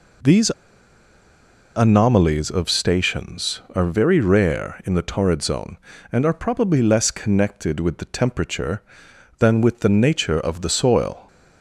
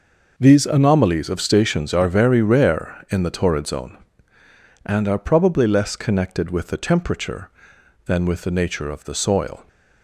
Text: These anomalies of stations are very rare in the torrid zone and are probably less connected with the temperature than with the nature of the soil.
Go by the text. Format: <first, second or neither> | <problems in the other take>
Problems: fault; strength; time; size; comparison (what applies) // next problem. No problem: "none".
second | pauses between "These" and "anomalies"; at 0.5 s; 1.2 s long